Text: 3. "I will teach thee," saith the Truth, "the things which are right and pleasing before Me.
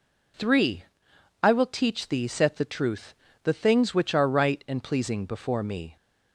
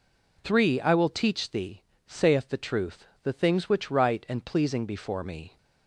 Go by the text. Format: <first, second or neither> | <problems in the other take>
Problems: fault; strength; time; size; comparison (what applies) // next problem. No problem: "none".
first | skips "are"; at 3.9 s